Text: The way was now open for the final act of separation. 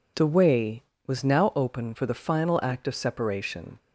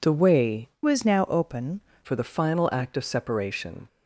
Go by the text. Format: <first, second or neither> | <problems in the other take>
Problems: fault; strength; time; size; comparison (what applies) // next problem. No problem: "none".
first | changes voice from "was" to "open"; from 0.8 to 1.8 s; 1.0 s long